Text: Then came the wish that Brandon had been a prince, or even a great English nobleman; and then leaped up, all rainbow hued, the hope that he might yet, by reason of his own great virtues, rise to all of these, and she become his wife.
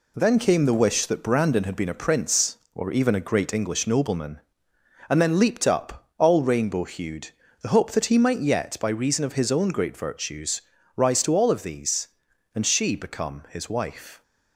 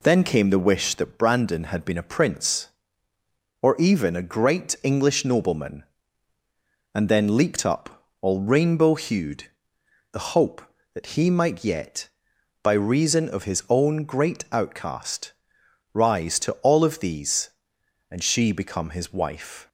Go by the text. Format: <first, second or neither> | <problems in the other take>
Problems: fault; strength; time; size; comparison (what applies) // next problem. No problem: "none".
first | says "outcast" for "virtues"; at 14.4 s